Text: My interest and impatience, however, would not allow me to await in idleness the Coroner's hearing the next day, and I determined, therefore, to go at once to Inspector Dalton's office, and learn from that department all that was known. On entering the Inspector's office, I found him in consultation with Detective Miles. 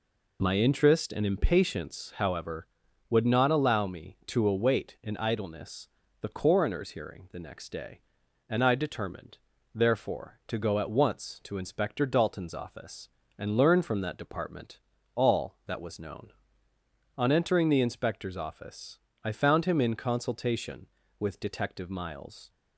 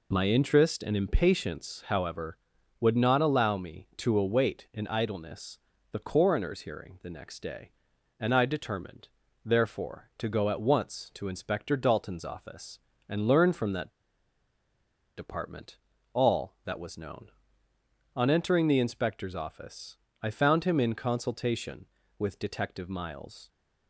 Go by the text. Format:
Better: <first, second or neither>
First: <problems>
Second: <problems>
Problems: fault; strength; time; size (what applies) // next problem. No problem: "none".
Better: first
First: pauses between "idleness" and "the"; slight; at 5.8 s; 0.34 s long // pauses between "department" and "all"; slight; at 14.7 s; 0.36 s long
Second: pauses between "idleness" and "the"; slight; at 5.5 s; 0.34 s long // pauses between "that" and "department"; strong; at 13.8 s; 1.2 s long // pauses between "department" and "all"; slight; at 15.7 s; 0.36 s long